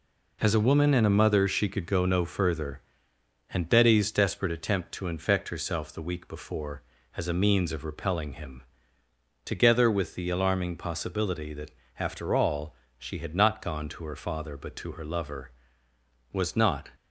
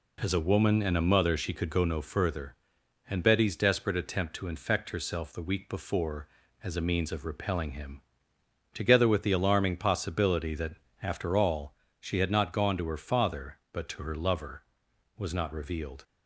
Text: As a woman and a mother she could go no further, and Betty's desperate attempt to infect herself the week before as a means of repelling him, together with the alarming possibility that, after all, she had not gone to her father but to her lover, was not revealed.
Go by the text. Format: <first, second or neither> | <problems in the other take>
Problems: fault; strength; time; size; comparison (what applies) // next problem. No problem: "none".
second | stops before "revealed"; at 16.9 s